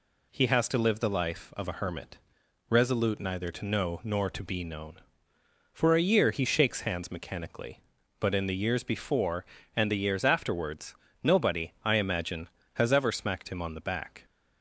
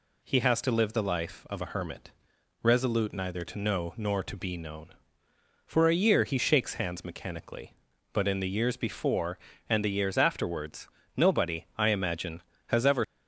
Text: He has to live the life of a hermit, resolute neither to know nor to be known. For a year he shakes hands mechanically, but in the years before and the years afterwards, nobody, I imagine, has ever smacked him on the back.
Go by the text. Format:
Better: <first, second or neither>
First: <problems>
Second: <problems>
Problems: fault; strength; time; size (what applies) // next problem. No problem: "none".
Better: first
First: none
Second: stops before "smacked him on the back"; at 13.0 s